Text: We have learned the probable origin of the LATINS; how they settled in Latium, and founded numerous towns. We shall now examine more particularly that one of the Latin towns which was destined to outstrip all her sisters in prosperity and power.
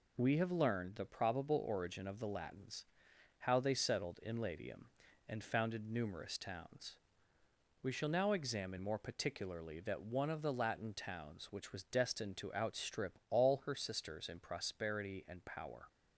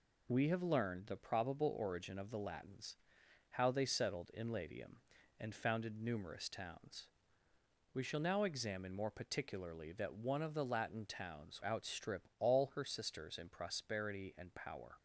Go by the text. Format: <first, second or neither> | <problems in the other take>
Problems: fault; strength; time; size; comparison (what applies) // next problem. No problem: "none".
first | skips "which was destined to"; at 11.6 s